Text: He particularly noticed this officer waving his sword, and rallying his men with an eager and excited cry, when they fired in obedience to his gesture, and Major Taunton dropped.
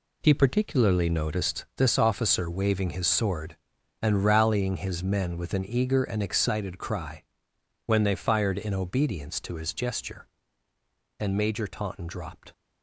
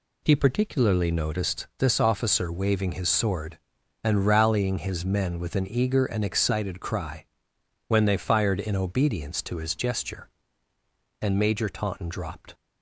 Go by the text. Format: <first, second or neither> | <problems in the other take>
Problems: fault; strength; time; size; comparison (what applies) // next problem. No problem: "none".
second | gets quieter; strong; throughout; 9 dB